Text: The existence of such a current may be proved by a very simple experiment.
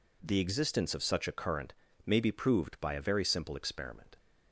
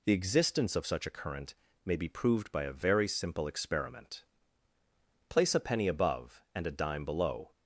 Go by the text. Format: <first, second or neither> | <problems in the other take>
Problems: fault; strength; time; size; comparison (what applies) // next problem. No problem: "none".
first | pauses between "current" and "may"; slight; at 1.5 s; 0.30 s long; slight in the first // goes on to say "Place a penny above and a dime below"; strong; from 5.2 s on; 2.2 s long